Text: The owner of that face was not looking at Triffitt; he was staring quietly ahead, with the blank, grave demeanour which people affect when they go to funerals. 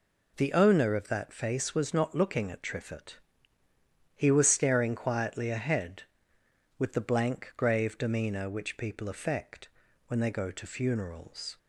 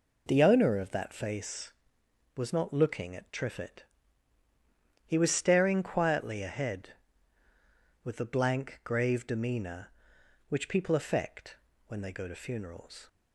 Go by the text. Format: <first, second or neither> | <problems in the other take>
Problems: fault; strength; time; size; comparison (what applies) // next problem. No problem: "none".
neither | pauses between "affect" and "when"; the same in both